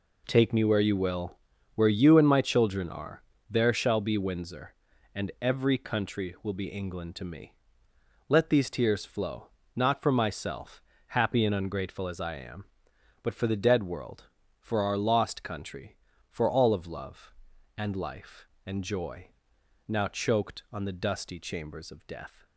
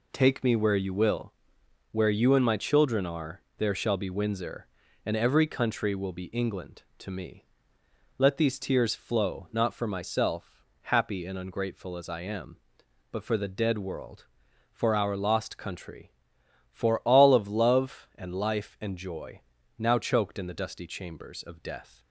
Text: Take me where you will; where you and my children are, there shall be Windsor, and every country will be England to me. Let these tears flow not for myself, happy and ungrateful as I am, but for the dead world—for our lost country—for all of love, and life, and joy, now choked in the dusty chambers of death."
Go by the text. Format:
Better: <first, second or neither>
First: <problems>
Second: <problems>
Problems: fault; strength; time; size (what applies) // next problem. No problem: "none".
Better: second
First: pauses between "flow" and "not"; slight; at 9.4 s; 0.30 s long // says "on" for "in"; at 20.7 s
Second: none